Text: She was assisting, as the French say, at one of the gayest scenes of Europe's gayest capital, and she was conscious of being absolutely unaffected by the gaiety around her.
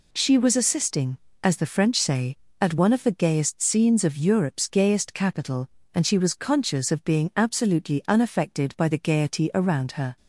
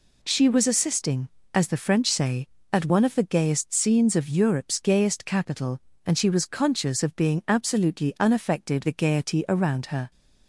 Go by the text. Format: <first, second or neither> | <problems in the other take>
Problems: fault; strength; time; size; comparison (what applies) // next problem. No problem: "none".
first | skips "by"; at 8.8 s